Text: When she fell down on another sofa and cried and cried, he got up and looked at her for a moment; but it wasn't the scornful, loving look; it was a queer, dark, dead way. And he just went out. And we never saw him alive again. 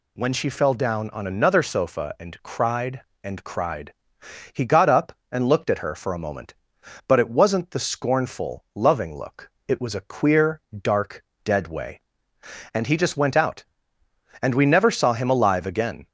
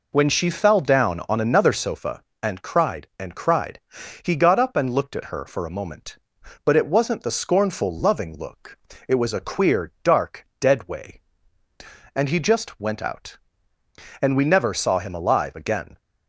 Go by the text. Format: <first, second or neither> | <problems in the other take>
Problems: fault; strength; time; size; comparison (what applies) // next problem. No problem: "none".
neither | none